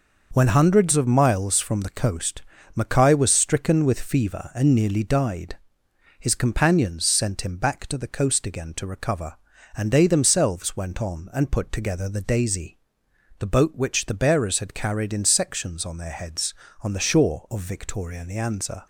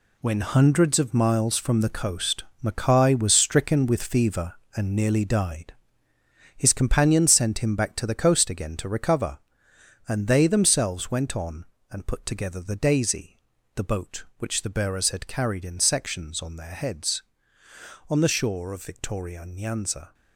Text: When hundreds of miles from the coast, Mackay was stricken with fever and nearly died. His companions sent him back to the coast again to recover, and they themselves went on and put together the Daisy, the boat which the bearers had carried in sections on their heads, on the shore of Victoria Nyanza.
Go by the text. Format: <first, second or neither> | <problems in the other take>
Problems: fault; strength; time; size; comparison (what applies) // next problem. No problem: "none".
first | gets quieter; strong; throughout; 9.5 dB